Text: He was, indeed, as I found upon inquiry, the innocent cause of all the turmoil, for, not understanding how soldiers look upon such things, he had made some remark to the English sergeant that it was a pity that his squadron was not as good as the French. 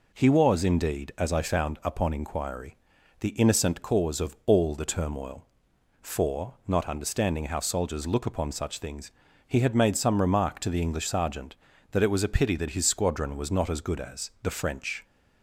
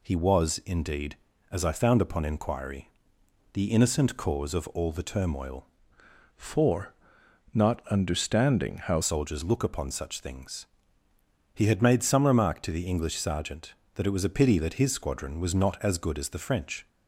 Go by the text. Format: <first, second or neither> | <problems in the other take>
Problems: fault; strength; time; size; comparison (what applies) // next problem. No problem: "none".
first | changes voice from "for" to "how"; from 6.3 to 9.0 s; 2.7 s long